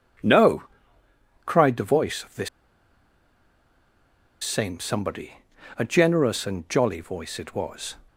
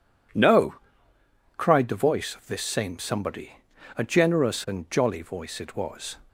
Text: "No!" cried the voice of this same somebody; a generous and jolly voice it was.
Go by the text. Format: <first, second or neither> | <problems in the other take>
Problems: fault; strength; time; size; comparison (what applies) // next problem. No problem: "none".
second | pauses between "this" and "same"; strong; at 2.4 s; 1.9 s long